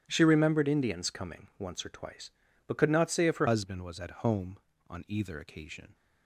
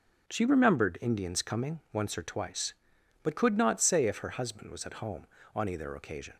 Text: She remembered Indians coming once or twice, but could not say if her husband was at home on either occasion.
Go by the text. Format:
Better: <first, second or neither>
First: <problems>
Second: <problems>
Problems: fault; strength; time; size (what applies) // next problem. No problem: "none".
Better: second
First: starts louder than the rest; strong; until 1.0 s; 11.5 dB // changes voice at "husband"; from 3.4 s on; 2.5 s long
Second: starts louder than the rest; until 1.3 s; 6.5 dB